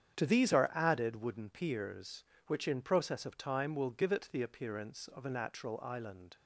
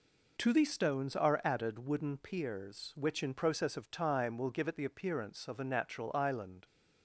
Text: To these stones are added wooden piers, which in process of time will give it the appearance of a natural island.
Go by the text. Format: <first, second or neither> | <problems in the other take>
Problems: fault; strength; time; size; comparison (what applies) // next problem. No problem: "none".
second | starts louder than the rest; strong; until 1.2 s; 8.5 dB // skips "stones"; at 0.5 s